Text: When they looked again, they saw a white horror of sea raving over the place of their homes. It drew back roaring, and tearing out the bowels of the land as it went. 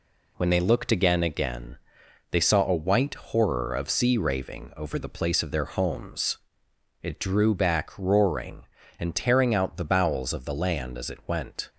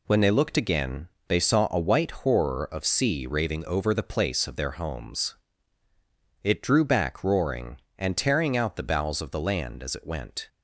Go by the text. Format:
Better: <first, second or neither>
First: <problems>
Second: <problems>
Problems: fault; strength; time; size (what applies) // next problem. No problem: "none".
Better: second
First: says "again" twice; at 1.2 s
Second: none